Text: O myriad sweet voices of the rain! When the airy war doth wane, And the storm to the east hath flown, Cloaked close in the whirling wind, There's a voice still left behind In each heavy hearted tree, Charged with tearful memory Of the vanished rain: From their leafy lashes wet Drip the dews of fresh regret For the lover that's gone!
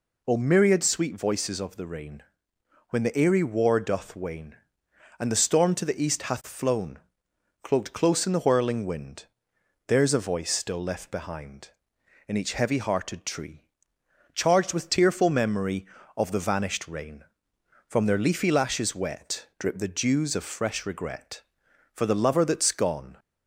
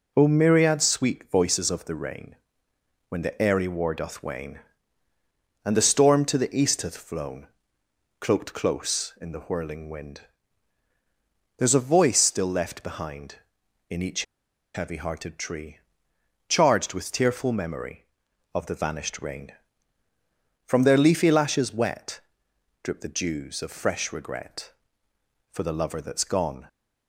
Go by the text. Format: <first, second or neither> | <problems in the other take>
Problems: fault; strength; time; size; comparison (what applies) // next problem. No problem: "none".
first | pauses between "each" and "heavy"; noticeable; at 14.2 s; 0.51 s long // pauses between "wet" and "Drip"; noticeable; at 22.2 s; 0.62 s long